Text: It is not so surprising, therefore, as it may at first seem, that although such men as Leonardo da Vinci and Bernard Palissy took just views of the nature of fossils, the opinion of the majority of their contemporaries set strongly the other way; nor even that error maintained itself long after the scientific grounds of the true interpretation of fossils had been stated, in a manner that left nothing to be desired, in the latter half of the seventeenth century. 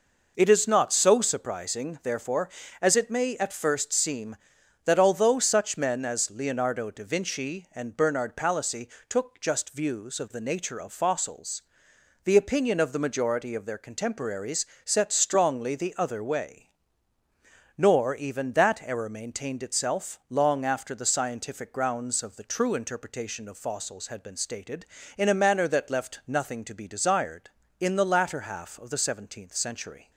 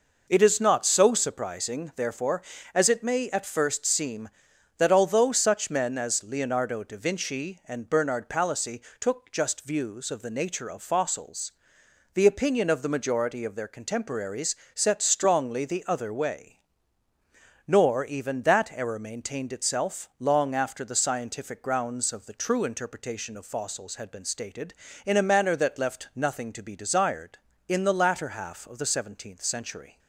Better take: neither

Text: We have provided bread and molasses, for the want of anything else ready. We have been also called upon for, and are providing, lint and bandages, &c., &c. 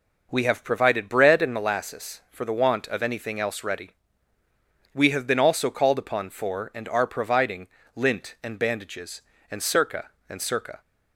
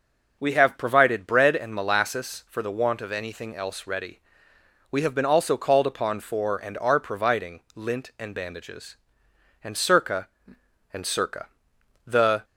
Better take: first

